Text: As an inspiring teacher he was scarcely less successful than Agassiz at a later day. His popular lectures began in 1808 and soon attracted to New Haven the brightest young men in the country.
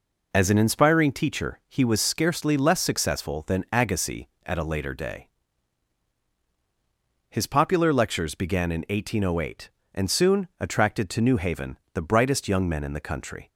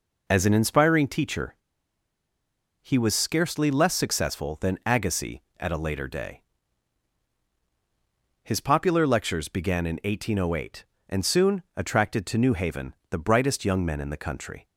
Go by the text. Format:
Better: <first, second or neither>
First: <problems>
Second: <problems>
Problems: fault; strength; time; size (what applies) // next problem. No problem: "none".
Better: first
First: pauses between "Haven" and "the"; slight; at 11.7 s; 0.16 s long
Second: pauses between "teacher" and "he"; strong; at 1.5 s; 1.2 s long // pauses between "soon" and "attracted"; slight; at 11.6 s; 0.16 s long // pauses between "Haven" and "the"; slight; at 12.9 s; 0.16 s long